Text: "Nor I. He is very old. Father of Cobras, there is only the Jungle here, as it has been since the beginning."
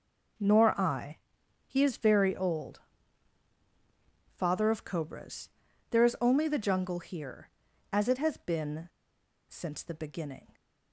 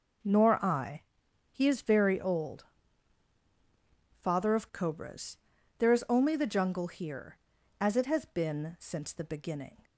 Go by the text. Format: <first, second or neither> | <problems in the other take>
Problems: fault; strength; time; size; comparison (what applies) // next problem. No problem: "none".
second | pauses between "been" and "since"; noticeable; at 8.8 s; 0.60 s long